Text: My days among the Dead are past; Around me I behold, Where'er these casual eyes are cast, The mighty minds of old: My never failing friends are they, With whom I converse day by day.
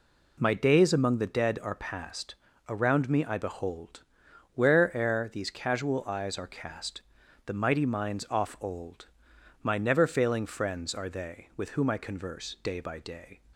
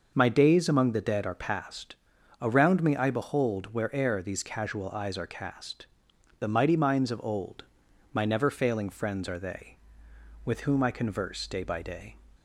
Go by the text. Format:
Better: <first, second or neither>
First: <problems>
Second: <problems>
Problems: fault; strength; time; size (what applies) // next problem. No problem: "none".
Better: second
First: says "off" for "of"; at 8.3 s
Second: none